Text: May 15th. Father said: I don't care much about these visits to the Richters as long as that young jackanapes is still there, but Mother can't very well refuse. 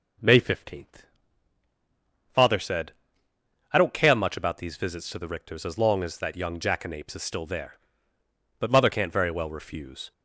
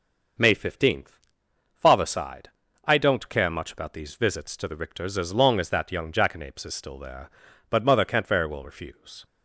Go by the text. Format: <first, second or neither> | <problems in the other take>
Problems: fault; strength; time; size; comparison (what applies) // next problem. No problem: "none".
first | starts louder than the rest; noticeable; until 1.9 s; 6 dB // says "sighed" for "said"; at 2.0 s